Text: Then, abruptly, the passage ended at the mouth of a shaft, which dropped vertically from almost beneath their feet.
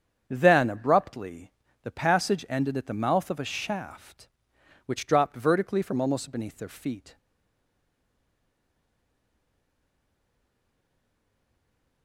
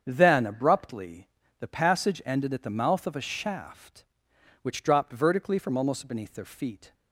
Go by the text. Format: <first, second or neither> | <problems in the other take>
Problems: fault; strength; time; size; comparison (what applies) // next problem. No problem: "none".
second | starts louder than the rest; strong; until 1.2 s; 7.5 dB; strong in the second // stays silent after the last word; strong; from 7.1 s on; 4.9 s long